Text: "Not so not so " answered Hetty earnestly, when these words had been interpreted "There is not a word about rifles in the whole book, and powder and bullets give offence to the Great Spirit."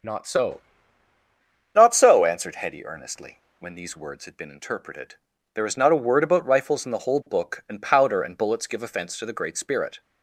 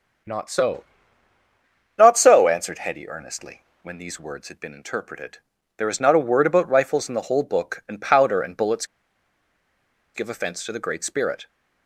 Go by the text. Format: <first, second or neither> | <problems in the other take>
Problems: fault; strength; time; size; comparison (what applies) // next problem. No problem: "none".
first | starts louder than the rest; until 2.3 s; 7 dB; also in the first // pauses between "so" and "not"; at 0.8 s; 1.1 s long; also in the first // pauses between "interpreted" and "There"; slight; at 5.3 s; 0.36 s long; slight in the first // pauses between "bullets" and "give"; strong; at 8.8 s; 1.2 s long